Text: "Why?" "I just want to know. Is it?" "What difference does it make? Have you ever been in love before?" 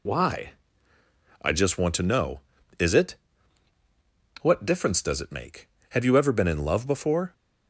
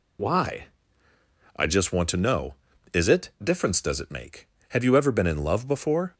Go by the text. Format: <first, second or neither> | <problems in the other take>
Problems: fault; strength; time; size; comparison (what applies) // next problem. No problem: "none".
first | skips "What"; at 3.3 s